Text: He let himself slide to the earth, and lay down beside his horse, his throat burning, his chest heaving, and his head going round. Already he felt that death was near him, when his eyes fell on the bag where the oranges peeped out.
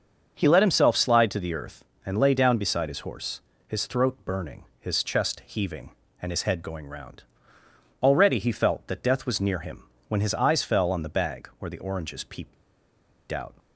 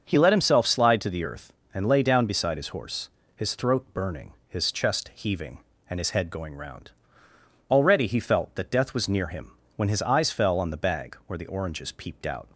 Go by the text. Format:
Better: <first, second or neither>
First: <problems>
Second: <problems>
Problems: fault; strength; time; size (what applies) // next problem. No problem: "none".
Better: second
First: starts louder than the rest; until 1.3 s; 6 dB // pauses between "peeped" and "out"; noticeable; at 12.5 s; 0.77 s long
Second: starts louder than the rest; noticeable; until 1.0 s; 6 dB